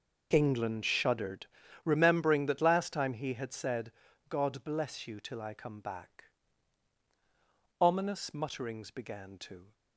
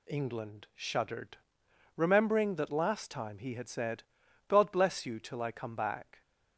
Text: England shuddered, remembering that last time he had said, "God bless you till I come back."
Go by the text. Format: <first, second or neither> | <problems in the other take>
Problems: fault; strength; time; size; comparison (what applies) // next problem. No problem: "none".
second | goes on to say "Ominous mutterings began to"; strong; from 7.8 s on; 1.9 s long